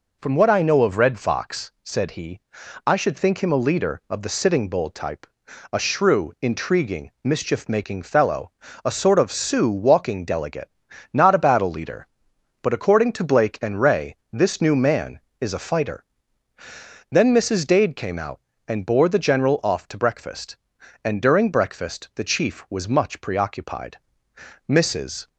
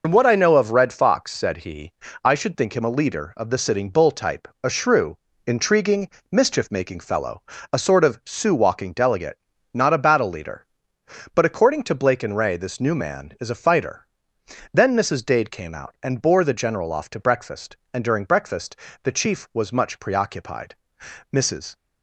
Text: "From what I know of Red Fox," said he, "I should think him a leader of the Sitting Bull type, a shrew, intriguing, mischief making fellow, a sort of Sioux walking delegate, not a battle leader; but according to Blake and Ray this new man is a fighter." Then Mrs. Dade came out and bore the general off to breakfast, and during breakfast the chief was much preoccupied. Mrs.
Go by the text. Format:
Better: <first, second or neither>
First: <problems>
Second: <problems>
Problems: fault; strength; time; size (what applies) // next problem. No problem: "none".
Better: first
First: none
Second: loses the start of "From"; at 0.0 s; 75 ms // pauses between "breakfast" and "the"; slight; at 18.7 s; 0.26 s long